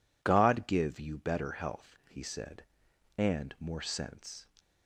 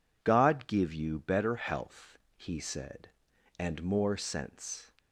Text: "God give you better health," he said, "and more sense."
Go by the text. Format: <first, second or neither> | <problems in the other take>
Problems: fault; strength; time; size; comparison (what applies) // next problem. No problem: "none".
neither | none